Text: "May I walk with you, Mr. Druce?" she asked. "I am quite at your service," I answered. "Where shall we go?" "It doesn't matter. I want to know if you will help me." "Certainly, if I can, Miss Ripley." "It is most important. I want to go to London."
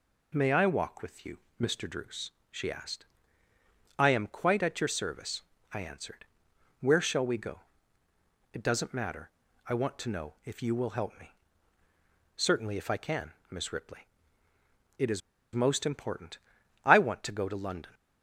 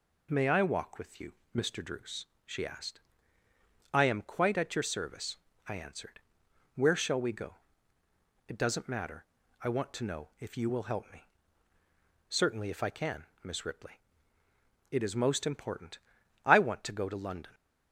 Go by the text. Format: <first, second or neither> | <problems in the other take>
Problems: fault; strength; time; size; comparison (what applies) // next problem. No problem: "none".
second | pauses between "is" and "most"; slight; at 15.2 s; 0.33 s long